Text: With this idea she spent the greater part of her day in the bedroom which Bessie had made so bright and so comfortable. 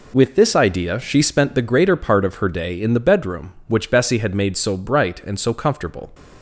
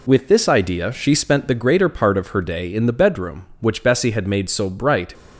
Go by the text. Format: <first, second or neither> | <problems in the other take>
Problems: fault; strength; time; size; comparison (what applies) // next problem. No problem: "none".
first | stops before "and so comfortable"; at 5.1 s